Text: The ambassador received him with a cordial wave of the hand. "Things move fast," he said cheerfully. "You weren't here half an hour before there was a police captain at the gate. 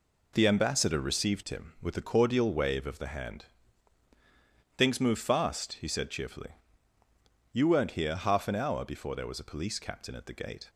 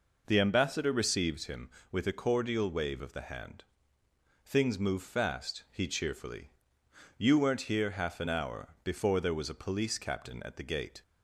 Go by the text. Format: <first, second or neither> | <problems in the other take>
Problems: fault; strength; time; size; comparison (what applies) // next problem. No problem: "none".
first | skips "said"; at 5.8 s